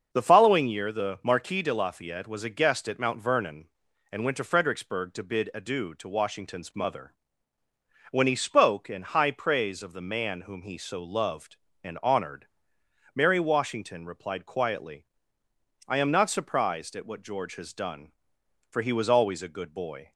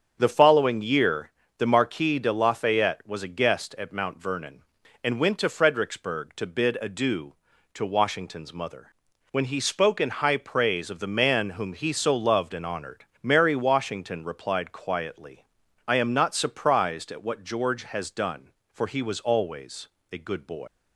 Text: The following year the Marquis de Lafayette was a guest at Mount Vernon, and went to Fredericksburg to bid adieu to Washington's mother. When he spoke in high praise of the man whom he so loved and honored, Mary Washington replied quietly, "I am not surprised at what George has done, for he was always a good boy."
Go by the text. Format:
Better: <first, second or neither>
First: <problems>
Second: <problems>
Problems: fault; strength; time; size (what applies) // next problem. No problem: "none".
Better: first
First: starts louder than the rest; until 1.1 s; 6.5 dB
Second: starts louder than the rest; strong; until 1.2 s; 7.5 dB // pauses between "year" and "the"; slight; at 1.2 s; 0.30 s long // pauses between "always" and "a"; slight; at 19.8 s; 0.22 s long // leaves "boy" unfinished; at 20.6 s; 110 ms